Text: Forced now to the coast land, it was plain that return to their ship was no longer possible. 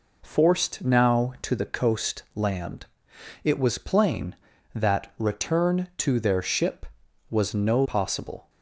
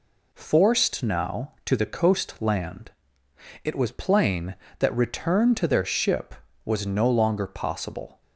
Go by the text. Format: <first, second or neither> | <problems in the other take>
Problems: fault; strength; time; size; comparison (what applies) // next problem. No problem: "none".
second | skips "longer"; at 7.8 s